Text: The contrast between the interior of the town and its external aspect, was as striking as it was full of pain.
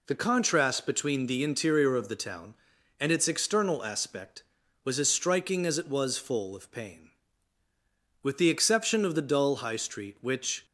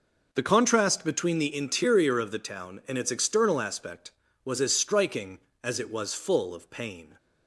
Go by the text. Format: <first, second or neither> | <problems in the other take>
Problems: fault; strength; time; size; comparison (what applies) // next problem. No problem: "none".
second | goes on to say "With the exception of the dull high street which"; strong; from 8.2 s on; 2.4 s long